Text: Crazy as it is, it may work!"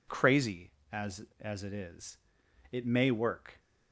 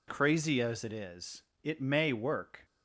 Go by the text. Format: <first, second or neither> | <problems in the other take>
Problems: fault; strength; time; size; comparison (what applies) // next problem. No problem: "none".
second | says "as" twice; at 1.3 s